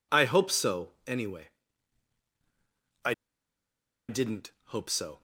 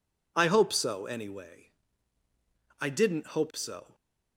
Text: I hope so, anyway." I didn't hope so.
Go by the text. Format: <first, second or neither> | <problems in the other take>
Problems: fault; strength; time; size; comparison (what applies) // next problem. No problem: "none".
second | pauses between "I" and "didn't"; noticeable; at 3.1 s; 0.96 s long